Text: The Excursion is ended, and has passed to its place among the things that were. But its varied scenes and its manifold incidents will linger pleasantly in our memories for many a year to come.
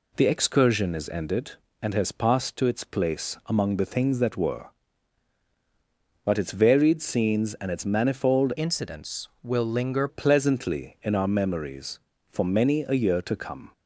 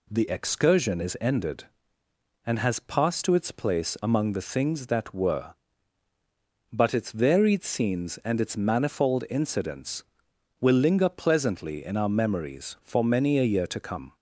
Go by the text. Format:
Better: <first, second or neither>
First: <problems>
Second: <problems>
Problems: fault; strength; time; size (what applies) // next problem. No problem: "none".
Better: second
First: changes voice from "incidents" to "linger"; from 8.5 to 10.0 s; 1.5 s long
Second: none